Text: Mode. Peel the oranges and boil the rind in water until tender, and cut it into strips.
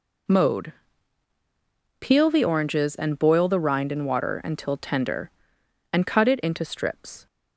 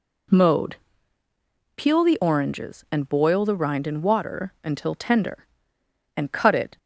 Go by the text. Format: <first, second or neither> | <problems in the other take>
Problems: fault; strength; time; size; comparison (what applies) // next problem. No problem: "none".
first | stops before "into strips"; at 6.7 s